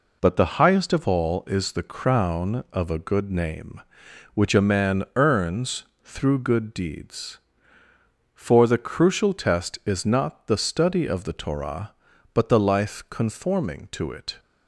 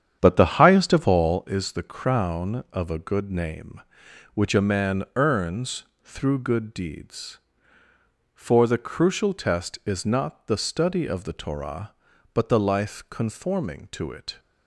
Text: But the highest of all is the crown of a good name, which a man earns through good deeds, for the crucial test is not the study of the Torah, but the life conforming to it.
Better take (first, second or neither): first